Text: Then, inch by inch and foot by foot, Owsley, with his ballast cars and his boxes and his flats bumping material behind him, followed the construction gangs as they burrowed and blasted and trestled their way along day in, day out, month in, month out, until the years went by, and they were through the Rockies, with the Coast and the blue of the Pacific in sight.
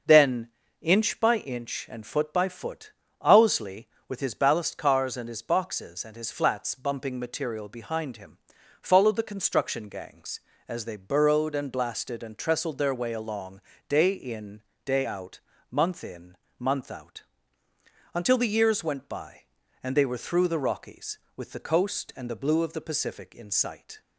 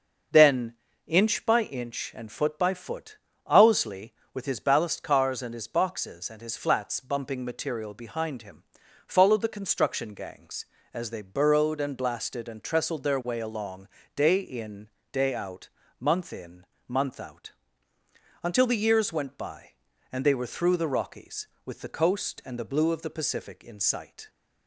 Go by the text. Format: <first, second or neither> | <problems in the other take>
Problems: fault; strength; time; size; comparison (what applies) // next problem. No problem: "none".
neither | starts louder than the rest; the same in both // pauses between "along" and "day"; slight; the same in both